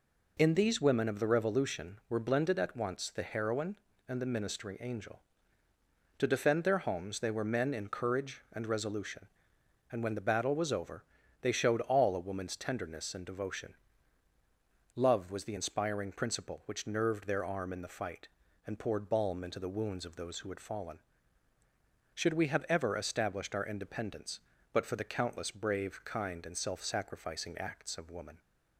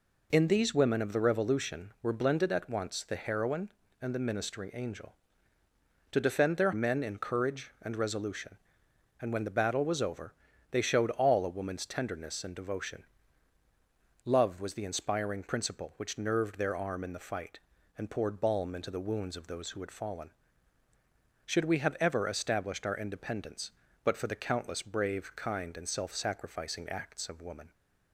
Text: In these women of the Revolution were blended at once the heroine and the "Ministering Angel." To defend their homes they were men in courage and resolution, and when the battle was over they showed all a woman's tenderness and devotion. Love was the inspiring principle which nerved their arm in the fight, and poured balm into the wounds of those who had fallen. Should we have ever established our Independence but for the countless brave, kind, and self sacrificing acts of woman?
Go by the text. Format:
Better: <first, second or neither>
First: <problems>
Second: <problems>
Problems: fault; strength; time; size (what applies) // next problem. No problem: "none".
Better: first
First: pauses between "over" and "they"; at 11.0 s; 0.40 s long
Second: skips "homes they were"; at 6.7 s // pauses between "over" and "they"; at 10.3 s; 0.40 s long